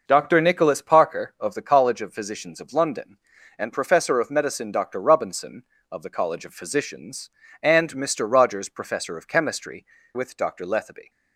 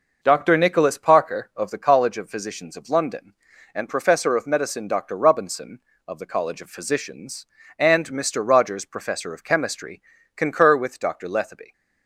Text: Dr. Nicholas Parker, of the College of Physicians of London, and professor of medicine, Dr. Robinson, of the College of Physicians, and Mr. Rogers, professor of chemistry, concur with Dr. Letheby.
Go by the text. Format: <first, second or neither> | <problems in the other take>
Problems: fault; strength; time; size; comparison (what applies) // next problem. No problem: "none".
second | skips "concur"; at 9.9 s